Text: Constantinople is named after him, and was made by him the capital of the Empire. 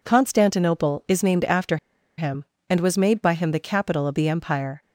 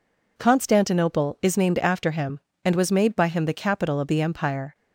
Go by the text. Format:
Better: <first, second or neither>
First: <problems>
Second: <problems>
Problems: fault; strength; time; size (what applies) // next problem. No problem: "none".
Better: second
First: pauses between "after" and "him"; at 1.7 s; 0.41 s long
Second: none